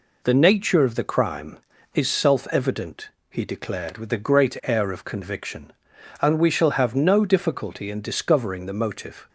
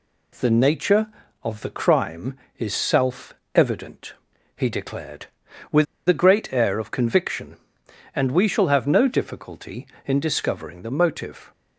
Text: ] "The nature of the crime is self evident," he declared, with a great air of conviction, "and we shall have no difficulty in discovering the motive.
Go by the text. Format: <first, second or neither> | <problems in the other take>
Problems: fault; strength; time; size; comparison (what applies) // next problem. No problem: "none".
first | pauses between "self" and "evident"; slight; at 3.3 s; 0.18 s long // pauses between "with" and "a"; slight; at 5.8 s; 0.21 s long